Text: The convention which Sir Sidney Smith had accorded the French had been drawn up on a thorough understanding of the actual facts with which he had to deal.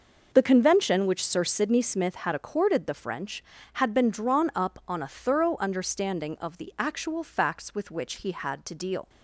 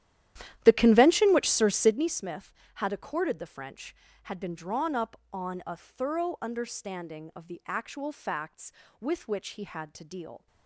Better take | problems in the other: first | starts louder than the rest; strong; until 2.1 s; 12 dB

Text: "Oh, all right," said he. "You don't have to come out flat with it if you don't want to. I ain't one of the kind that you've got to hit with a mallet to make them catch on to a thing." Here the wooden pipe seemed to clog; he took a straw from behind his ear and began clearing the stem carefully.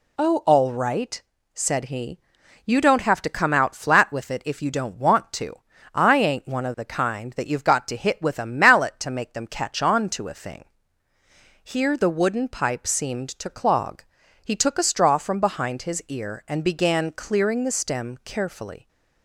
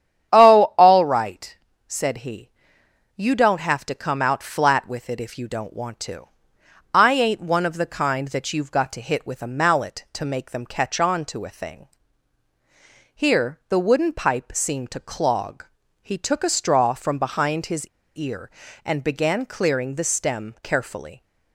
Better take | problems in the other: first | starts louder than the rest; strong; until 1.3 s; 9.5 dB // pauses between "his" and "ear"; slight; at 17.8 s; 0.28 s long

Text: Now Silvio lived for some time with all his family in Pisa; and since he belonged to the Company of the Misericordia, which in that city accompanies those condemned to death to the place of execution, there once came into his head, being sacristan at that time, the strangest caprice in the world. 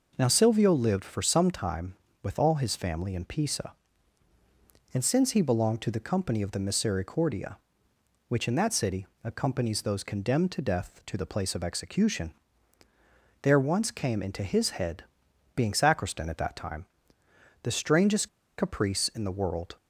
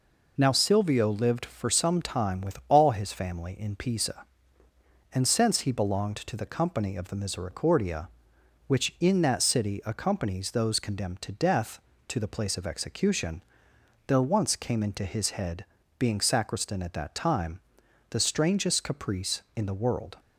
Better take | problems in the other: second | pauses between "city" and "accompanies"; slight; at 9.0 s; 0.16 s long // pauses between "strangest" and "caprice"; slight; at 18.2 s; 0.29 s long

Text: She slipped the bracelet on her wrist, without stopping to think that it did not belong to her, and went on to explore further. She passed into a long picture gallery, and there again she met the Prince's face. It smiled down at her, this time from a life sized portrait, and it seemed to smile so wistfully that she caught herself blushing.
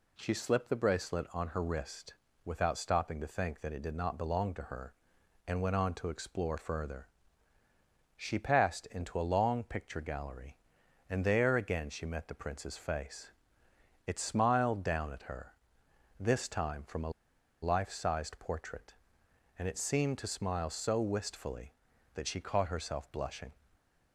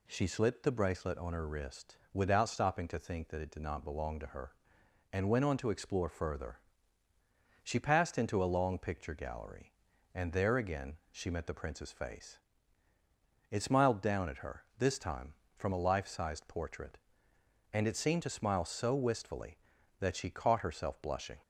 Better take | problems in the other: second | pauses between "a" and "life"; noticeable; at 17.1 s; 0.51 s long

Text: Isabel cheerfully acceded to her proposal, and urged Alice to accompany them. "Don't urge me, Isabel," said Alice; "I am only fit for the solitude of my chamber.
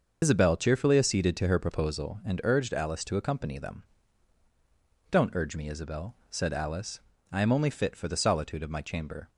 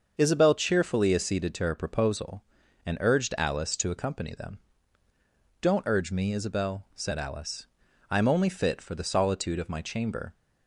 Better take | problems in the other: second | loses the start of "Isabel"; at 0.2 s; 105 ms // starts louder than the rest; noticeable; until 1.2 s; 6 dB; also in the second

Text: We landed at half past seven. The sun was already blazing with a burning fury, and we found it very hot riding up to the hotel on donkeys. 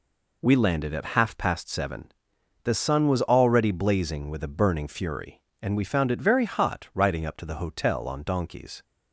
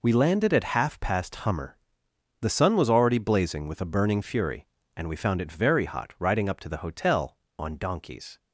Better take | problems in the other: first | says "hummer" for "seven"; at 1.3 s

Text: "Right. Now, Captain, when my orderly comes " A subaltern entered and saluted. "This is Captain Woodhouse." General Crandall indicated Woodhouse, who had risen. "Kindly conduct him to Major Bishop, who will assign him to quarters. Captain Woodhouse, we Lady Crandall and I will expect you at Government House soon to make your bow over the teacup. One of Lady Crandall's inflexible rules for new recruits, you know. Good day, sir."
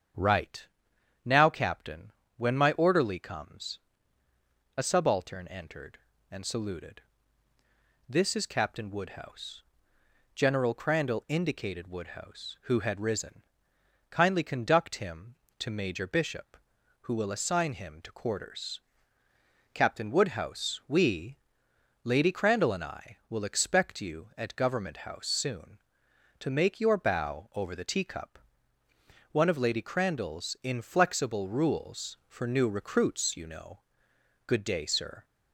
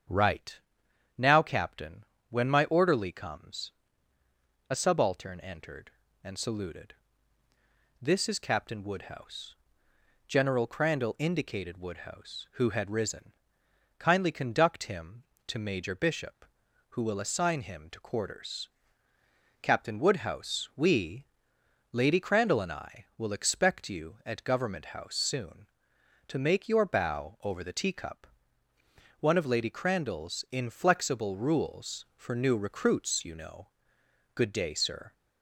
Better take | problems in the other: neither | starts louder than the rest; strong; the same in both // pauses between "we" and "Lady"; noticeable; the same in both

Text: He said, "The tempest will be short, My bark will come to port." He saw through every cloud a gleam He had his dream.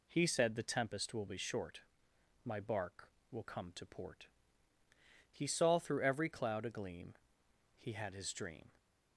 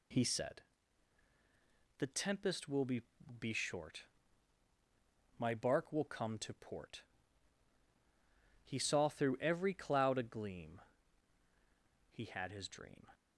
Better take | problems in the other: first | says "be" twice; at 3.3 s // pauses between "gleam" and "He"; strong; at 10.8 s; 1.2 s long; noticeable in the first

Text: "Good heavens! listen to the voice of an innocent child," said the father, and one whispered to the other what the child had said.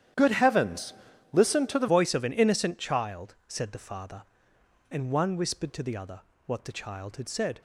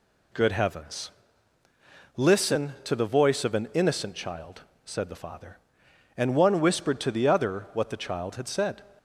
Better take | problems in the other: second | starts louder than the rest; strong; until 1.5 s; 10 dB // changes voice at "voice"; from 1.8 s on; 5.8 s long // pauses between "other" and "what"; slight; at 6.1 s; 0.28 s long

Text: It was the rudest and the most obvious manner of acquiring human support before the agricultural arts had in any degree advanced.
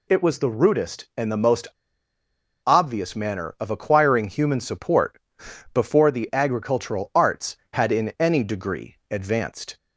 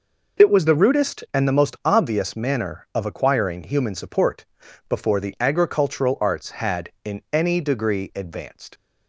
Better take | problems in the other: second | pauses between "most" and "obvious"; at 1.6 s; 1.0 s long // pauses between "support" and "before"; noticeable; at 5.2 s; 0.52 s long; also in the second

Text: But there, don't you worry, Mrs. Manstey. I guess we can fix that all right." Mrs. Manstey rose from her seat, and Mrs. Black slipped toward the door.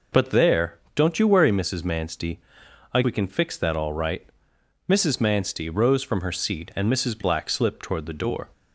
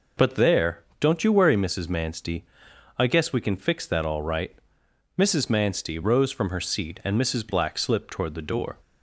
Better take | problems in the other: second | skips "guess"; at 3.0 s

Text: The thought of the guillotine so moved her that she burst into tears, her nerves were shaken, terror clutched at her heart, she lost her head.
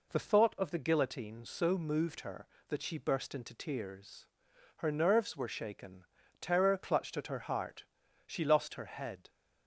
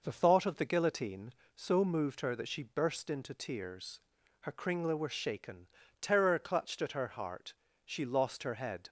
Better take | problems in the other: first | says "kringla" for "nerves"; at 4.5 s

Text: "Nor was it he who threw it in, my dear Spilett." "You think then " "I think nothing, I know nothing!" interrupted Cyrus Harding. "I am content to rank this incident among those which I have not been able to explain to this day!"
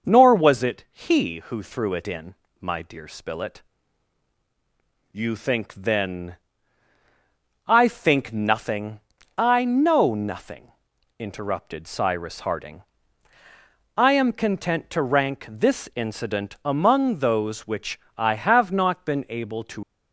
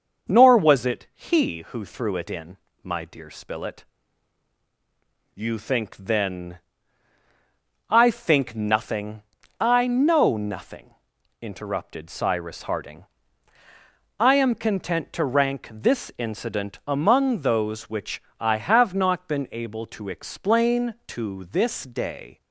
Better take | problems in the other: second | starts louder than the rest; until 1.1 s; 6 dB; also in the second // pauses between "which" and "I"; slight; at 17.9 s; 0.20 s long; slight in the second // stops before "explain to this day"; at 19.8 s

